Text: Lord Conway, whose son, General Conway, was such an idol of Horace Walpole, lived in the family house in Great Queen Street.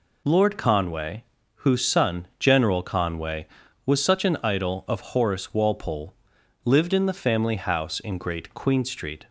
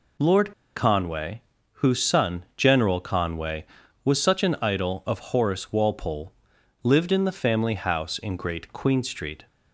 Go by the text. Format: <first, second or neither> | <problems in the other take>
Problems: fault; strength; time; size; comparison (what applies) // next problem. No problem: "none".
first | pauses between "Lord" and "Conway"; slight; at 0.5 s; 0.23 s long